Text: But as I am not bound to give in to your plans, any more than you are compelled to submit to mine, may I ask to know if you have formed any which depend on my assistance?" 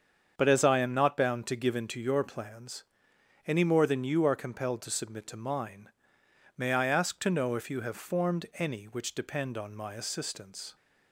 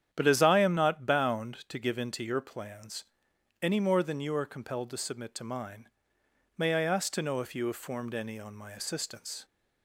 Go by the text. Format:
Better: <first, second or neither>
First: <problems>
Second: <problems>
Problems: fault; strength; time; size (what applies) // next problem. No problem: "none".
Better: first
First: starts louder than the rest; strong; until 1.3 s; 7.5 dB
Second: starts louder than the rest; strong; until 1.1 s; 9.5 dB // skips "which depend"; at 8.3 s